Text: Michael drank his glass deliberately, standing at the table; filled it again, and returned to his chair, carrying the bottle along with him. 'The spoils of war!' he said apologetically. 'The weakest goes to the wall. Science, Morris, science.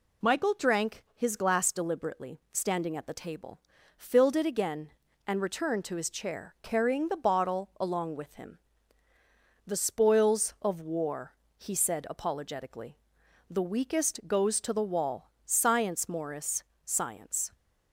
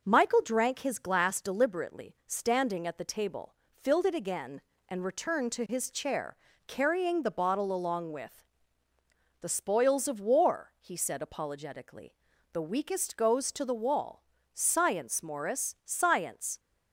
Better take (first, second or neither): first